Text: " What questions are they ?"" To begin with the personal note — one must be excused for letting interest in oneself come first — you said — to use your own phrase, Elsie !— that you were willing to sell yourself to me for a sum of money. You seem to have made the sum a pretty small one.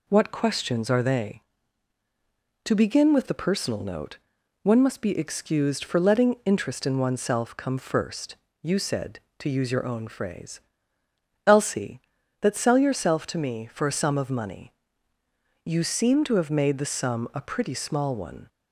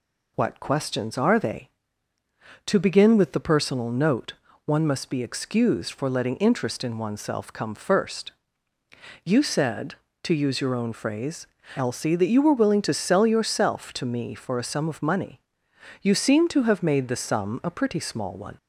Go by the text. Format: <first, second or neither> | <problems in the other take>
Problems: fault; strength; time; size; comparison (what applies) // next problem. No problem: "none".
second | skips "you were willing to"; at 12.5 s